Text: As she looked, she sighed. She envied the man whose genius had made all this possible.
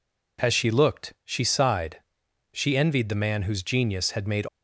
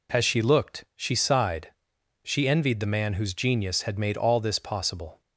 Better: second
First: stops before "all this possible"; at 4.4 s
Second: none

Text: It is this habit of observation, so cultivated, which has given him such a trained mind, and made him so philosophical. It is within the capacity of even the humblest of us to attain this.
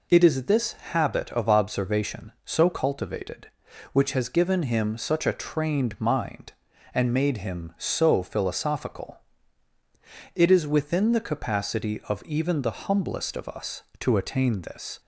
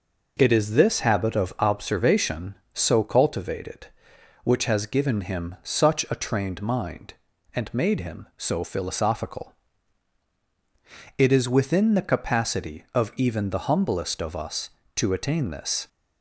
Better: neither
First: none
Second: none

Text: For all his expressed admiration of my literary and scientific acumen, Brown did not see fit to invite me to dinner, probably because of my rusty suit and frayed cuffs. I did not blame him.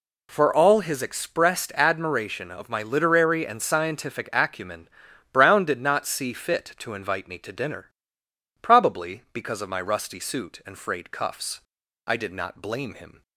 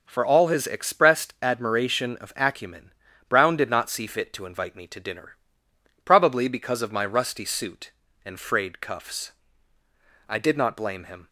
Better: first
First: none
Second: skips "my literary and scientific"; at 2.3 s

